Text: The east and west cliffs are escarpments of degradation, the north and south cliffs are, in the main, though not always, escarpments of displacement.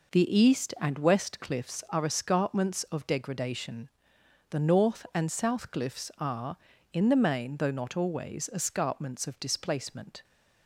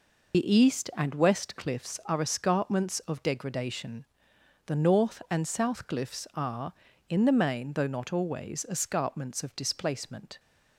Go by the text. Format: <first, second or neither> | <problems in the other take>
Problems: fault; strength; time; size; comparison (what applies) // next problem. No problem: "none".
first | loses the start of "The"; at 0.3 s; 75 ms